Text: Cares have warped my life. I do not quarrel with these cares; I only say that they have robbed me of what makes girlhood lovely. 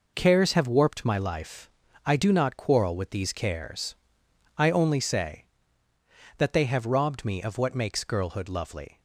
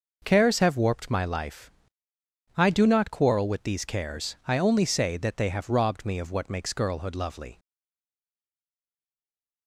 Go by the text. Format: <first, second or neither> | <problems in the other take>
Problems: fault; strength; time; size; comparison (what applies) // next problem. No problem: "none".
first | stays silent after the last word; noticeable; from 7.5 s on; 2.1 s long